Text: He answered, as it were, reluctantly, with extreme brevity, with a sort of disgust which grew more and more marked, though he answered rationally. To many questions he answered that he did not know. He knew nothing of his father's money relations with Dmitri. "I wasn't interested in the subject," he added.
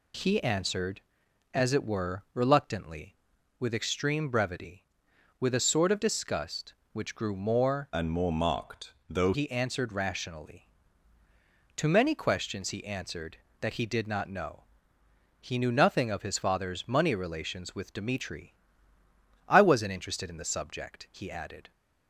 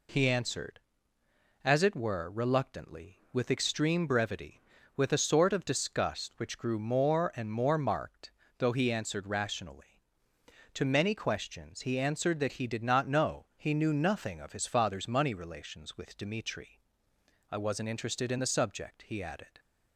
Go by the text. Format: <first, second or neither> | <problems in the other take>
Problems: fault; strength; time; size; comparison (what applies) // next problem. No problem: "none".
second | changes voice from "and" to "though"; from 7.9 to 9.3 s; 1.4 s long